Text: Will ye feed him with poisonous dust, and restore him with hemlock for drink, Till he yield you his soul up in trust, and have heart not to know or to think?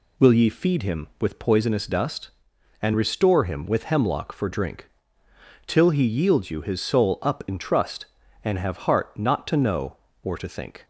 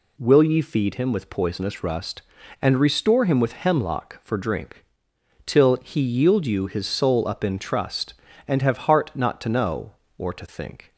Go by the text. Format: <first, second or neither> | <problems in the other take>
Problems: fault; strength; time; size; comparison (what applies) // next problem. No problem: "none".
first | says "rust" for "dust"; at 1.8 s